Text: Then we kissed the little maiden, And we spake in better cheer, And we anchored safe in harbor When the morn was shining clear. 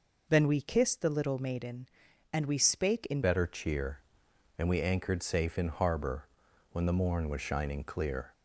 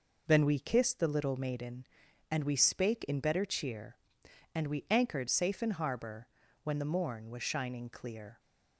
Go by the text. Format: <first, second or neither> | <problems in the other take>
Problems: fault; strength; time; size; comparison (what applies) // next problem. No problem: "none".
second | changes voice at "better"; from 3.2 s on; 5.1 s long // pauses between "harbor" and "When"; noticeable; at 6.2 s; 0.48 s long; slight in the second